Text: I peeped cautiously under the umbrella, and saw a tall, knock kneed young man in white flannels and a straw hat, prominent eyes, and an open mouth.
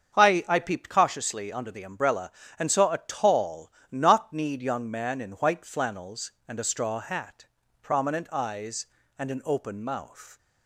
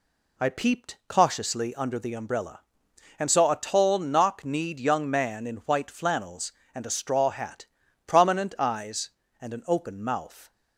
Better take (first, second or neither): second